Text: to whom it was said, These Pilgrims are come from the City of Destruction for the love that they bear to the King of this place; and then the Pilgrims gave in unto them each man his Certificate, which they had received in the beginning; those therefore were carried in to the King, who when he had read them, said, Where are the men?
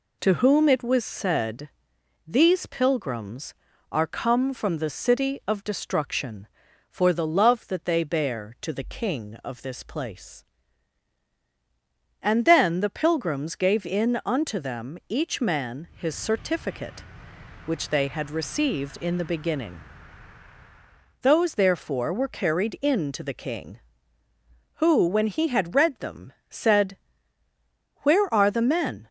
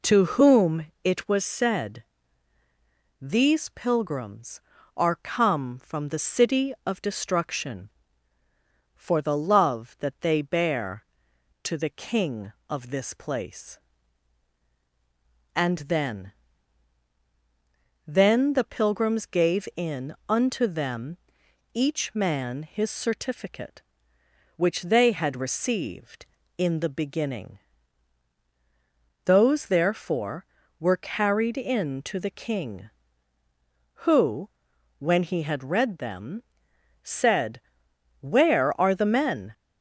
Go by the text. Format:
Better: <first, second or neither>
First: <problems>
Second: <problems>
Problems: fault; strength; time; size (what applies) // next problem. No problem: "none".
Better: first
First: none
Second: pauses between "whom" and "it"; slight; at 0.8 s; 0.16 s long // says "then" twice; at 18.0 s // pauses between "them" and "each"; noticeable; at 21.1 s; 0.56 s long // pauses between "who" and "when"; noticeable; at 34.4 s; 0.50 s long